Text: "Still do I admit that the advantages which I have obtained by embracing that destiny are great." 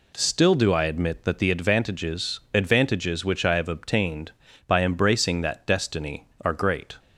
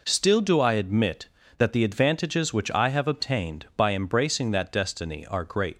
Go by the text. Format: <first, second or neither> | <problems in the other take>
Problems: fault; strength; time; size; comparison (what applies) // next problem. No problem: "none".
second | says "advantages" twice; at 2.5 s